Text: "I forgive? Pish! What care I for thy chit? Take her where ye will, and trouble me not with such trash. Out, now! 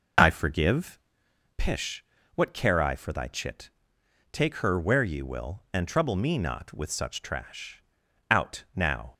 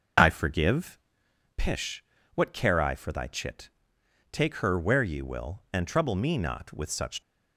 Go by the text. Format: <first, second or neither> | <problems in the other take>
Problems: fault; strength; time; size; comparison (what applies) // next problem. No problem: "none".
first | stops before "trash Out now"; at 7.2 s